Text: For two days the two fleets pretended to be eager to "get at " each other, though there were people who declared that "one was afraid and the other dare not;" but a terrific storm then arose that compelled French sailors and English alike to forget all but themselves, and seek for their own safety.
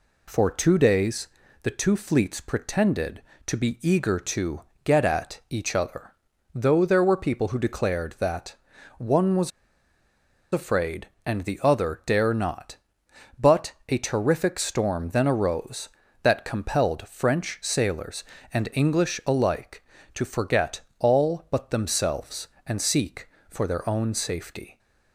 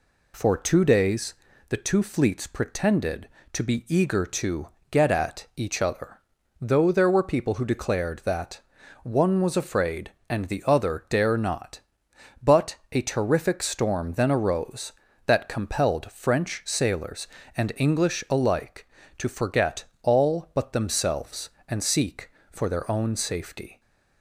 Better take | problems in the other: second | pauses between "days" and "the"; slight; at 1.2 s; 0.36 s long; slight in the second // pauses between "to" and "get"; slight; at 4.6 s; 0.24 s long; slight in the second // pauses between "that" and "one"; at 8.5 s; 0.44 s long; also in the second // pauses between "was" and "afraid"; at 9.5 s; 1.0 s long // pauses between "forget" and "all"; slight; at 20.8 s; 0.18 s long; slight in the second

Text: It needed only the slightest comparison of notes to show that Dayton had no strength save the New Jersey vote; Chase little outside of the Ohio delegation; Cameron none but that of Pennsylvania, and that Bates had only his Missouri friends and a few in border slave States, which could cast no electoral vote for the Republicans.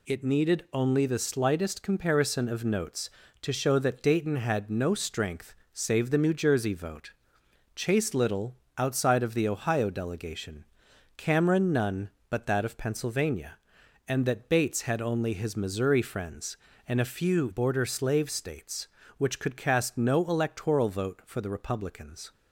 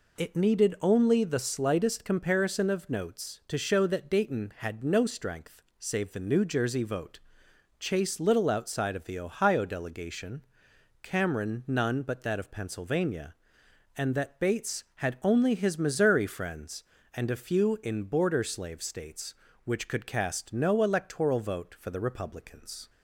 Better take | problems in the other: second | pauses between "strength" and "save"; slight; at 5.5 s; 0.20 s long; slight in the second // pauses between "little" and "outside"; slight; at 8.5 s; 0.22 s long // skips "in"; at 17.4 s

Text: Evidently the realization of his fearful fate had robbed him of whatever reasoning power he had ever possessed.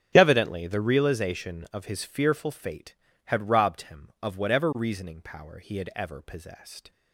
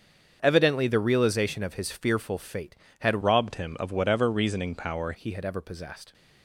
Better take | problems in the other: first | starts louder than the rest; strong; until 1.4 s; 7 dB; strong in the first // changes voice from "robbed" to "power"; from 3.2 to 5.1 s; 1.9 s long

